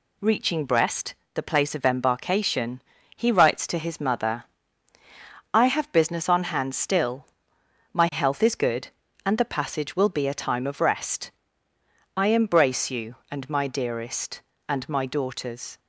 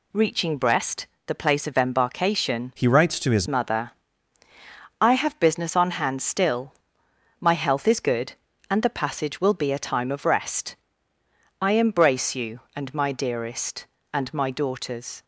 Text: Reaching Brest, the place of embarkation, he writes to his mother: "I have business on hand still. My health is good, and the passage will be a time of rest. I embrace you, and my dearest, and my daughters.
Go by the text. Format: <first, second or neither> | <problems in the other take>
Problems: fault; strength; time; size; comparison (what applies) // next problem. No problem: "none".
first | changes voice from "he" to "his"; from 2.7 to 3.4 s; 0.7 s long